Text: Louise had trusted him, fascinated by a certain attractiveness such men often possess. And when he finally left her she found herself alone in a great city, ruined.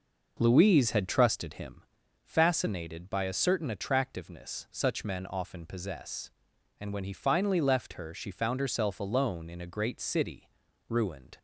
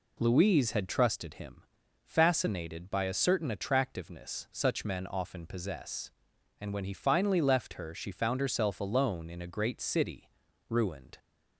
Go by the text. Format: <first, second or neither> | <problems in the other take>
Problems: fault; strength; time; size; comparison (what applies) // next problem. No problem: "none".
second | starts louder than the rest; noticeable; until 1.9 s; 5.5 dB